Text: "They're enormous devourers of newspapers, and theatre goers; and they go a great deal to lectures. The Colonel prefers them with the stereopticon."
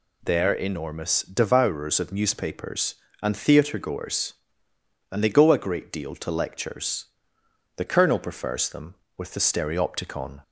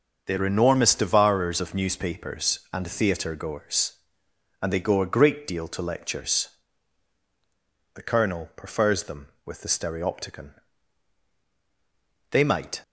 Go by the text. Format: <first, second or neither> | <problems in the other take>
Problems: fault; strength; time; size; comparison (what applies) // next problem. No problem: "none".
first | starts louder than the rest; until 1.2 s; 6 dB // goes on to say "They might"; from 12.3 s on; 0.52 s long